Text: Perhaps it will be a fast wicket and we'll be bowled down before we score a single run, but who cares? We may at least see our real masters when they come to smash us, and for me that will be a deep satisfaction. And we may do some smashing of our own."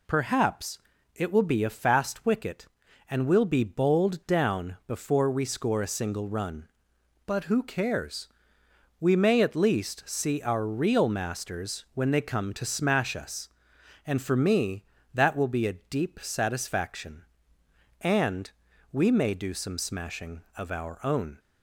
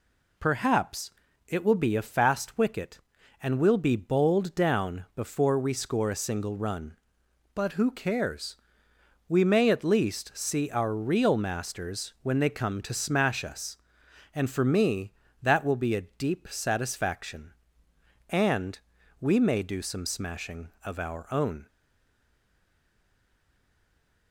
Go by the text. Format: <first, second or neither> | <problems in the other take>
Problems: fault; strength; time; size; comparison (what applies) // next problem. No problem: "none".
first | pauses between "Perhaps" and "it"; slight; at 1.1 s; 0.36 s long; slight in the first // pauses between "And" and "we"; at 18.7 s; 0.40 s long; also in the first // stays silent after the last word; strong; from 21.6 s on; 2.7 s long